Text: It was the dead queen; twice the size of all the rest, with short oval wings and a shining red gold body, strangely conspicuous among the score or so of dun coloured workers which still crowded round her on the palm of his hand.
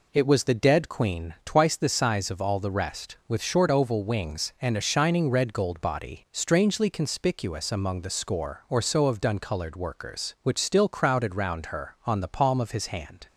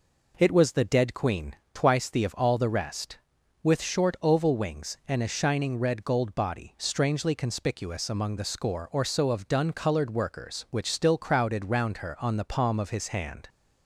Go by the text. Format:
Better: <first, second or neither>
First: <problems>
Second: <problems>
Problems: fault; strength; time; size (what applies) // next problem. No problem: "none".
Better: first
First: none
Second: skips "size"; at 2.2 s